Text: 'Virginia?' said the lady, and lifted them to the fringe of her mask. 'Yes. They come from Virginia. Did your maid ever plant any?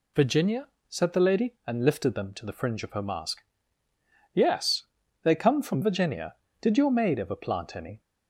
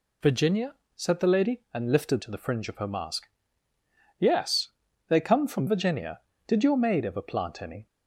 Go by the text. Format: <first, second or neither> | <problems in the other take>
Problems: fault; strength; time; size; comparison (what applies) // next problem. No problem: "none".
first | skips "them"; at 2.2 s